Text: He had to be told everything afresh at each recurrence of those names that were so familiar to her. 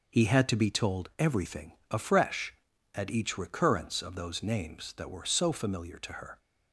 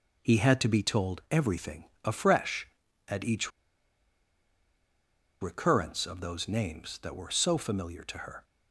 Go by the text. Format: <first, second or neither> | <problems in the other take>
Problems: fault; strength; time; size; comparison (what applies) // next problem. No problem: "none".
first | pauses between "everything" and "afresh"; slight; at 1.8 s; 0.20 s long; slight in the first // pauses between "each" and "recurrence"; strong; at 3.5 s; 1.9 s long